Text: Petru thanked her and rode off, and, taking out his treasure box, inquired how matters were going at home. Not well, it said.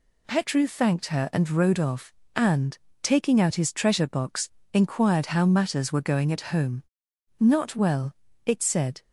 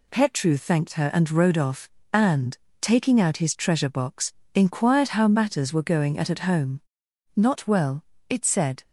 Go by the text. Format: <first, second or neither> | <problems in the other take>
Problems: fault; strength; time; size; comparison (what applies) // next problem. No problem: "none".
first | says "at" twice; at 6.3 s